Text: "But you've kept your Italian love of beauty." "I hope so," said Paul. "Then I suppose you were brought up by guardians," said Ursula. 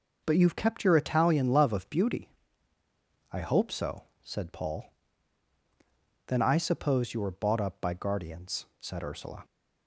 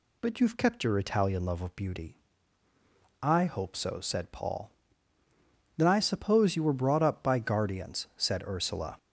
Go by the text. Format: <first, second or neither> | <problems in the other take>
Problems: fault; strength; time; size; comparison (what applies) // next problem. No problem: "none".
second | says "bought" for "brought"; at 7.3 s